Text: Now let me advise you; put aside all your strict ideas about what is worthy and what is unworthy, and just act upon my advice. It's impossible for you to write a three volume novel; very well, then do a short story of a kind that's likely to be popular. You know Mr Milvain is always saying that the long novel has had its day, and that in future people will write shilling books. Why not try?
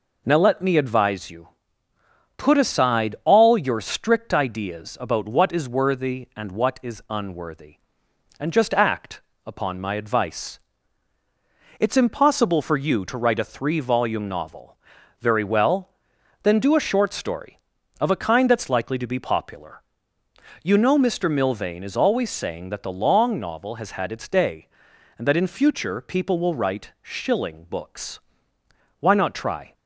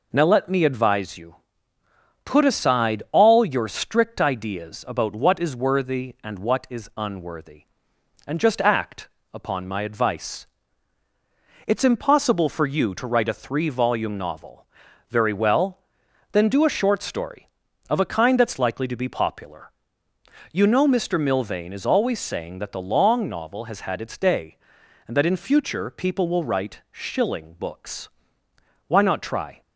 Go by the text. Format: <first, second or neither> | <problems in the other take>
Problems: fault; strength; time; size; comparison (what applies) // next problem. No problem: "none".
neither | pauses between "act" and "upon"; slight; the same in both